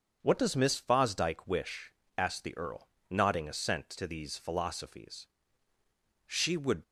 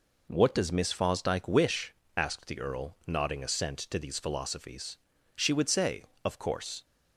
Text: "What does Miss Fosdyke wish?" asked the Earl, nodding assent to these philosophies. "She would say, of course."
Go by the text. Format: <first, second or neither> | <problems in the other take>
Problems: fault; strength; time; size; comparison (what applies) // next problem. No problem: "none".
second | starts louder than the rest; until 1.2 s; 6.5 dB // stops before "say of course"; at 6.8 s